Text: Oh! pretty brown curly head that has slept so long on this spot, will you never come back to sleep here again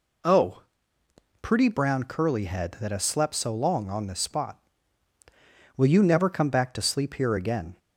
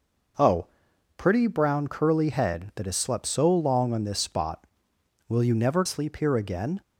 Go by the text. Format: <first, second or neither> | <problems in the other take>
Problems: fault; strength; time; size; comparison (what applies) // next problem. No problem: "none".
first | skips "come back to"; at 5.8 s